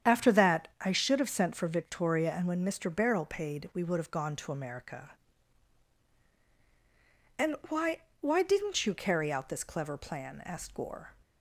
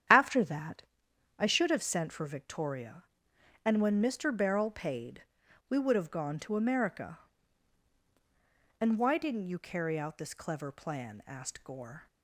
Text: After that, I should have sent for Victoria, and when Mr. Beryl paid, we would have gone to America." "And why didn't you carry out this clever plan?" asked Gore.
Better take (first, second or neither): second